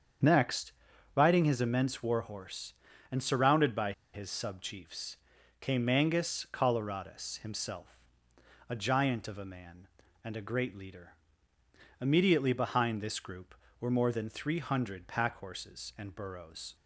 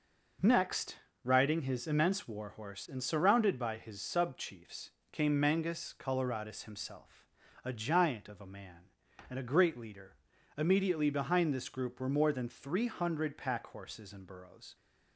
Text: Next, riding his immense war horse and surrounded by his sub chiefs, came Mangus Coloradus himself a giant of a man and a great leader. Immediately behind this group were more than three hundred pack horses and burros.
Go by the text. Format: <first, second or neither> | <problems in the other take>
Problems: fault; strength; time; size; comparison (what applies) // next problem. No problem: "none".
second | starts louder than the rest; strong; until 1.6 s; 7.5 dB // pauses between "by" and "his"; slight; at 3.9 s; 0.21 s long // pauses between "himself" and "a"; noticeable; at 7.9 s; 0.68 s long; slight in the second